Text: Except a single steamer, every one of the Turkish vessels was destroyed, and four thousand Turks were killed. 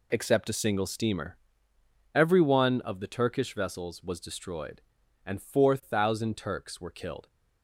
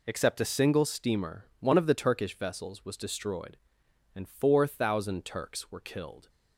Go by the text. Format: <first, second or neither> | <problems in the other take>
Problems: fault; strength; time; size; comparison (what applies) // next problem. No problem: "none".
first | skips "every"; at 1.5 s